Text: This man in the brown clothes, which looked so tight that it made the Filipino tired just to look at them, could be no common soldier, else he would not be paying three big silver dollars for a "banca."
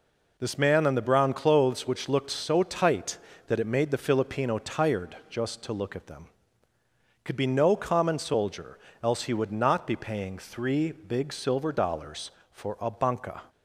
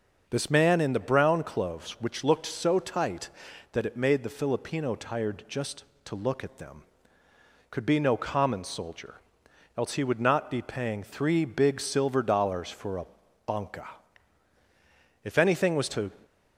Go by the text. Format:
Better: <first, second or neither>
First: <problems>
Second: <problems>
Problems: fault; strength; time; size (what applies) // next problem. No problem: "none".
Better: first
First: none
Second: starts louder than the rest; noticeable; until 1.2 s; 6 dB // pauses between "a" and "banca"; at 13.0 s; 0.40 s long // goes on to say "If anything was to"; noticeable; from 15.2 s on; 0.86 s long